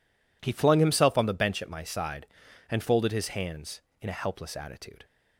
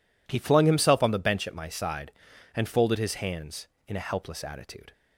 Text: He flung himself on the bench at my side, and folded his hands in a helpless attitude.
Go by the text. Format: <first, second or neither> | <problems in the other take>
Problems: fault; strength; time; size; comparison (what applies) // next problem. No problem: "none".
neither | none